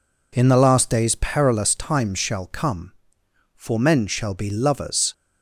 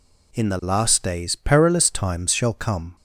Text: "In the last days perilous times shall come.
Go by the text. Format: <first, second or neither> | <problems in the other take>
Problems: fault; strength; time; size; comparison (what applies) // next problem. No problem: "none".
second | goes on to say "For men shall be lovers"; from 3.5 s on; 1.5 s long